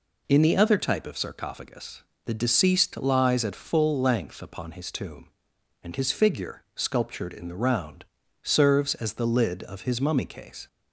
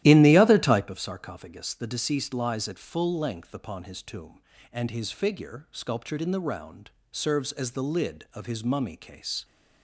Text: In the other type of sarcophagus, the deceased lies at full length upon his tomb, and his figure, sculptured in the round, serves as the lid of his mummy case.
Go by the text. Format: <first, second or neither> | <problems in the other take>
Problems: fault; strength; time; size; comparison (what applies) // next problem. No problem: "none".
first | starts louder than the rest; strong; until 0.9 s; 13.5 dB